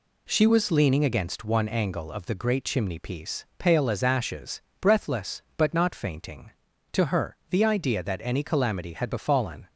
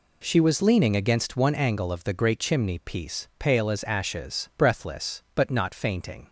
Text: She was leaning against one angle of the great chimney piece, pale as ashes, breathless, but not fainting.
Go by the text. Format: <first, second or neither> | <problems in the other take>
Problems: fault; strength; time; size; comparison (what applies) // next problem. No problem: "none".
second | goes on to say "To her the idea that any calamity had befallen"; strong; from 6.9 s on; 2.7 s long